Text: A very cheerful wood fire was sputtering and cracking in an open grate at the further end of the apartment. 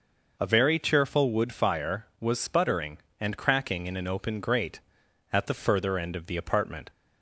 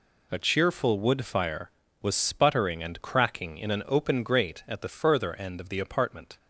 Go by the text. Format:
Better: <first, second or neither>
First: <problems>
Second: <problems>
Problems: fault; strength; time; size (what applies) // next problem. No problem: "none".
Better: first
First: none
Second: skips "very"; at 0.3 s